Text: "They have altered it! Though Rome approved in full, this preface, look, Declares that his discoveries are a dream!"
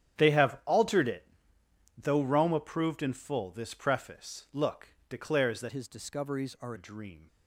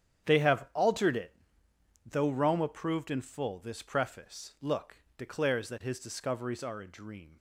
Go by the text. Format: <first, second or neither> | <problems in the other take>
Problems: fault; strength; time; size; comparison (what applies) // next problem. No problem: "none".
second | starts louder than the rest; strong; until 1.2 s; 9.5 dB; strong in the second // changes voice from "his" to "are"; from 5.6 to 6.7 s; 1.1 s long